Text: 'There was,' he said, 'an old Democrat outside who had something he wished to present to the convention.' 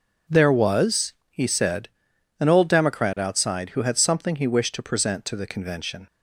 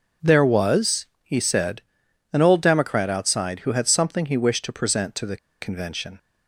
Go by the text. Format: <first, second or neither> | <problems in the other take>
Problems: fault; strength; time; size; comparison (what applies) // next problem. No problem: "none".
first | pauses between "the" and "convention"; slight; at 5.3 s; 0.24 s long